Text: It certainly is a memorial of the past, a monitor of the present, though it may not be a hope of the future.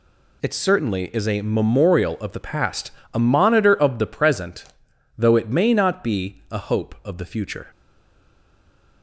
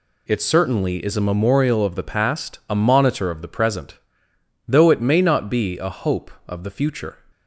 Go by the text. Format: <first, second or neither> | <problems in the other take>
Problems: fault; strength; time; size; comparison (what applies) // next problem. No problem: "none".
second | stays silent after the last word; noticeable; from 7.6 s on; 1.4 s long